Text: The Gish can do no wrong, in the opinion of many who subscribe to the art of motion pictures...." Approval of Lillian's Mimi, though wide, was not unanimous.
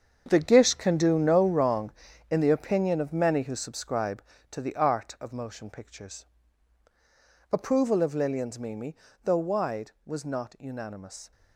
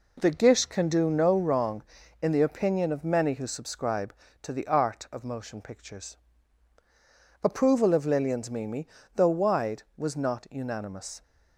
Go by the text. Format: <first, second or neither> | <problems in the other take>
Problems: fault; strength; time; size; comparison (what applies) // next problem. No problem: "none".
second | gets quieter; strong; throughout; 12 dB